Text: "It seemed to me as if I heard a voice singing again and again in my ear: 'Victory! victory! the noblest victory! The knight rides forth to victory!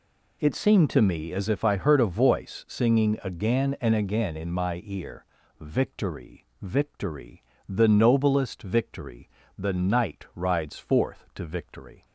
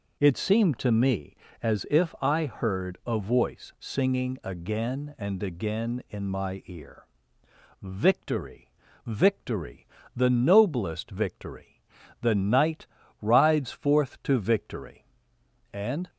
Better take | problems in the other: first | pauses between "knight" and "rides"; at 12.8 s; 0.38 s long // goes on to say "And"; slight; from 15.7 s on; 0.36 s long

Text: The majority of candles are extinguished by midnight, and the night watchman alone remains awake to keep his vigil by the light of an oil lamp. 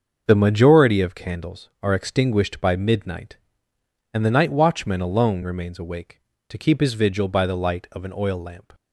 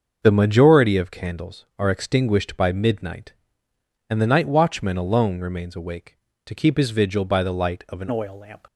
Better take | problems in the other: first | starts louder than the rest; until 1.2 s; 6.5 dB; also in the first // changes voice at "oil"; from 8.1 s on; 0.5 s long

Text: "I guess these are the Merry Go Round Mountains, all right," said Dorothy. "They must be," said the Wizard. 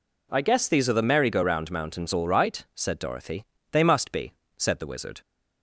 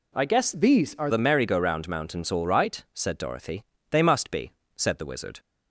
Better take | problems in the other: first | changes voice from "these" to "are"; from 0.5 to 1.0 s; 0.5 s long

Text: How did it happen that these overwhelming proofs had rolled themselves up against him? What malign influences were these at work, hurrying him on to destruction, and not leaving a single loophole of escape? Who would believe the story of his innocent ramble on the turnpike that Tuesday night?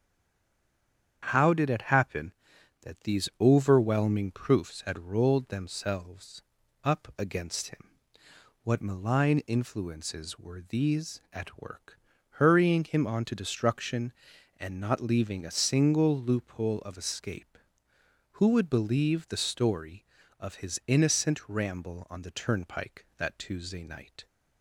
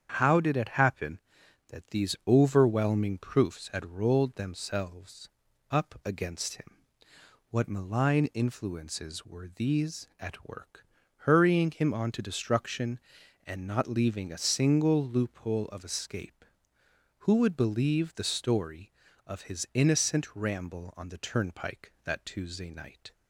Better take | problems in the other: second | stays silent before the first word; noticeable; until 1.2 s; 1.2 s long // starts louder than the rest; strong; until 2.2 s; 8.5 dB; strong in the second // pauses between "themselves" and "up"; at 6.4 s; 0.40 s long; also in the second

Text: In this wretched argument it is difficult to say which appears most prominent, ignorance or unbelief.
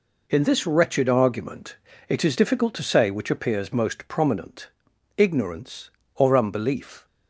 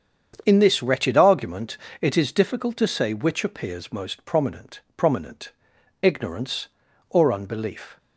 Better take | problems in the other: first | starts louder than the rest; strong; until 1.4 s; 7.5 dB // pauses between "argument" and "it"; slight; at 1.7 s; 0.22 s long; slight in the first // says "prominent" twice; at 4.9 s

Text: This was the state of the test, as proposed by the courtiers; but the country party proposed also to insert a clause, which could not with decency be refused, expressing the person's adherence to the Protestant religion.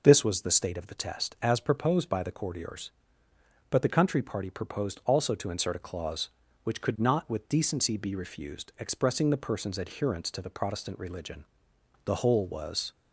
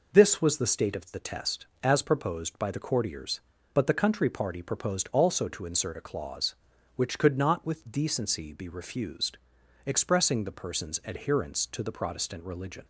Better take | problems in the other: second | goes on to say "The whole was"; noticeable; from 12.0 s on; 0.88 s long

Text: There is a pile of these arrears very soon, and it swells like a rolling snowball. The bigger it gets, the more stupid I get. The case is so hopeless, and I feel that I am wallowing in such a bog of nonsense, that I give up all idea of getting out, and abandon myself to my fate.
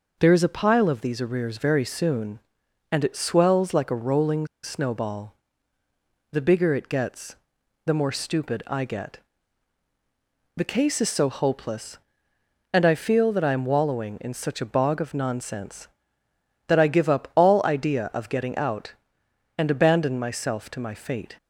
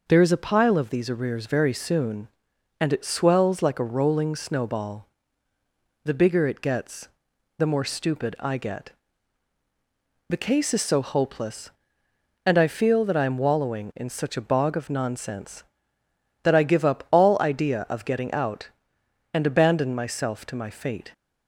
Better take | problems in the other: second | pauses between "rolling" and "snowball"; slight; at 4.4 s; 0.16 s long

